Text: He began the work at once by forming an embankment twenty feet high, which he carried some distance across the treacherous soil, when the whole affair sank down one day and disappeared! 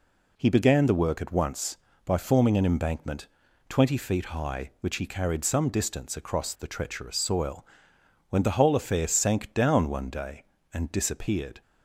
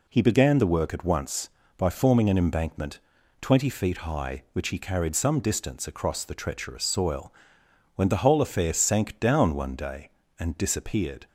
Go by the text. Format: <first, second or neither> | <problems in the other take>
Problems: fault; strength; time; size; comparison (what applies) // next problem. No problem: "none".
neither | pauses between "embankment" and "twenty"; the same in both